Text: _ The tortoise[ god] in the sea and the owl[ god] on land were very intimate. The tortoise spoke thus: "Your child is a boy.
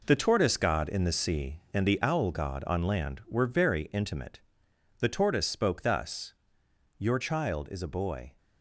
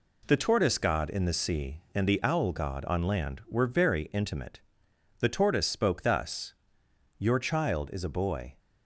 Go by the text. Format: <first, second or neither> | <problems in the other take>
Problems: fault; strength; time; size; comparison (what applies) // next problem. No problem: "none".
second | gets quieter; strong; throughout; 7.5 dB